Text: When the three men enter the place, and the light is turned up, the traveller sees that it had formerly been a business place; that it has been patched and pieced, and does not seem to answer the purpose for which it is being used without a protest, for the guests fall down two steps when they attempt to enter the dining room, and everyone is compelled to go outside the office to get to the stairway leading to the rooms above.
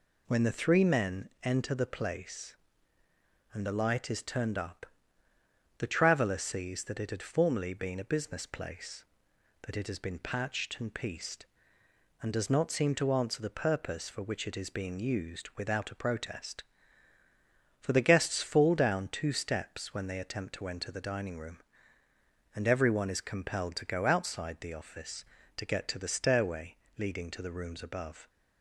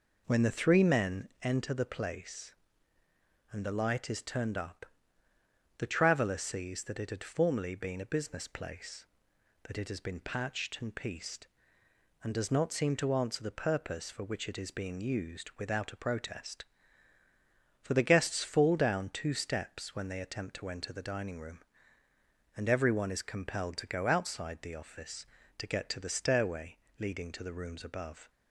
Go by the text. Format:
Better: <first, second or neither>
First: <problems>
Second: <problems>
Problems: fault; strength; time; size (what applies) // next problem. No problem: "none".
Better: first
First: pauses between "stairway" and "leading"; slight; at 26.7 s; 0.20 s long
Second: starts louder than the rest; noticeable; until 1.5 s; 4.5 dB // pauses between "stairway" and "leading"; slight; at 26.7 s; 0.20 s long